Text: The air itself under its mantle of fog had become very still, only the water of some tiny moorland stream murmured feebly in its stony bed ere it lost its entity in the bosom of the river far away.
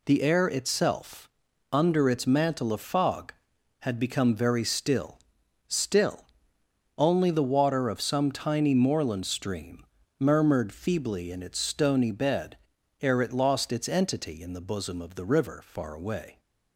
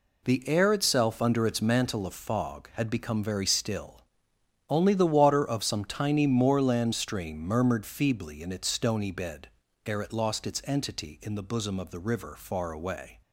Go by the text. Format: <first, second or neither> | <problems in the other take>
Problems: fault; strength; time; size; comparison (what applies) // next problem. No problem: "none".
second | pauses between "itself" and "under"; at 1.2 s; 0.44 s long // says "still" twice; at 5.6 s // pauses between "stream" and "murmured"; slight; at 9.8 s; 0.34 s long // pauses between "bed" and "ere"; at 12.5 s; 0.44 s long; also in the second